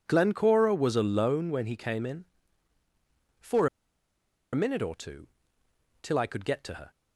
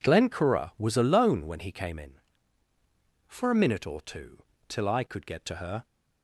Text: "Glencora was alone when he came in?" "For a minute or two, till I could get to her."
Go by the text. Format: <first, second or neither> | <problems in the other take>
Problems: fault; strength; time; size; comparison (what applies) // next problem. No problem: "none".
second | pauses between "For" and "a"; noticeable; at 3.6 s; 0.86 s long